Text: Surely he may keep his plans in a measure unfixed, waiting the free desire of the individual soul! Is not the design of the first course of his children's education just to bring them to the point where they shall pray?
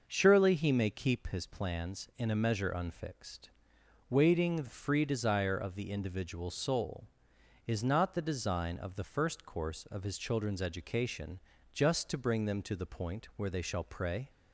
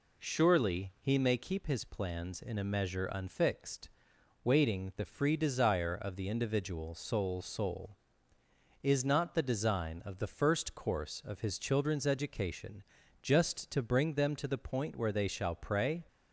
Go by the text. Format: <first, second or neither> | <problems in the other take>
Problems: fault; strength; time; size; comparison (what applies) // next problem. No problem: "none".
first | says "soul" twice; at 7.4 s // pauses between "education" and "just"; at 12.8 s; 0.40 s long; slight in the first